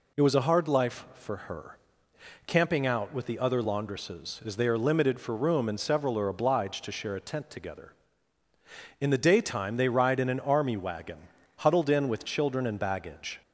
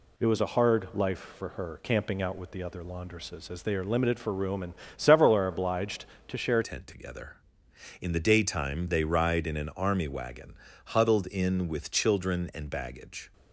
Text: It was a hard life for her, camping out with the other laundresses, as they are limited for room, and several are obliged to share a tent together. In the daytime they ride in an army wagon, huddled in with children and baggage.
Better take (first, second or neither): first